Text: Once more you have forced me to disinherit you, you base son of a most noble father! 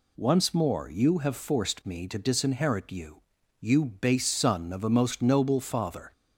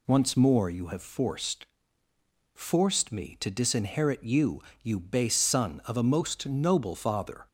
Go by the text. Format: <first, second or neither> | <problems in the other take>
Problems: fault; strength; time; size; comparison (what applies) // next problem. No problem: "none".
first | says "forced" twice; at 2.5 s